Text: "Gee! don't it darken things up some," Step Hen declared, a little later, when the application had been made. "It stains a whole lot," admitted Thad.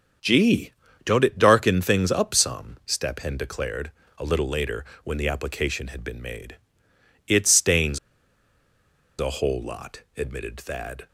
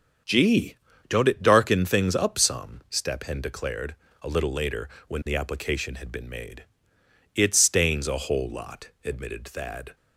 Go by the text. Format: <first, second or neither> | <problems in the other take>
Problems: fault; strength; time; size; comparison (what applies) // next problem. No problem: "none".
second | starts louder than the rest; until 1.5 s; 7 dB; also in the second // pauses between "stains" and "a"; at 7.9 s; 1.2 s long